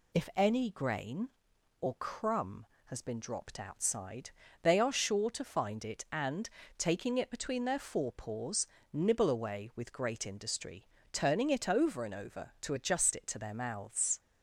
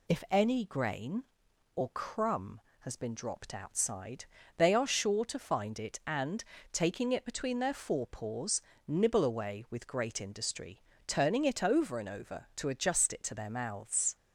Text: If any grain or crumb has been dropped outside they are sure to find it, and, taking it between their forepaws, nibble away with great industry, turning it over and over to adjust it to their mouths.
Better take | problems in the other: neither | pauses between "outside" and "they"; slight; the same in both

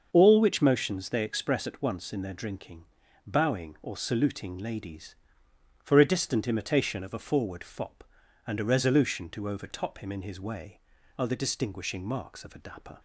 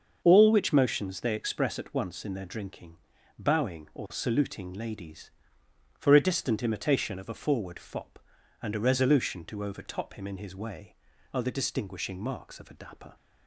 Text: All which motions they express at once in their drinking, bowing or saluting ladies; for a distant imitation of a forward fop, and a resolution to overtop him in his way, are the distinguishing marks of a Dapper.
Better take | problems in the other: neither | starts louder than the rest; the same in both

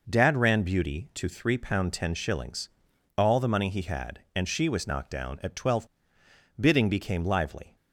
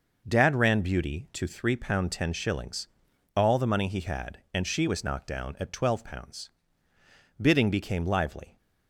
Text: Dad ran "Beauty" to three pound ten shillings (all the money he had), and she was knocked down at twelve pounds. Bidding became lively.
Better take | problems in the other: second | skips "pounds"; at 6.2 s

